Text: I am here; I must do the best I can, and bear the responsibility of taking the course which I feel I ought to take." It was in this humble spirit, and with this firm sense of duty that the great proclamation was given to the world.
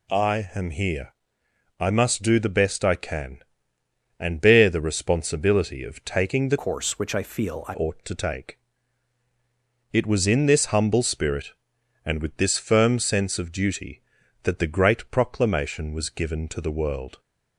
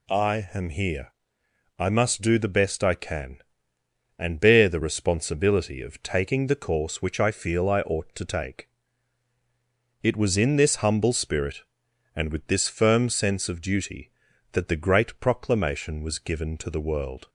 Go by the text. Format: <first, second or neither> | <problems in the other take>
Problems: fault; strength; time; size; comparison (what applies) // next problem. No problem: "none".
second | changes voice from "course" to "I"; from 6.5 to 7.7 s; 1.2 s long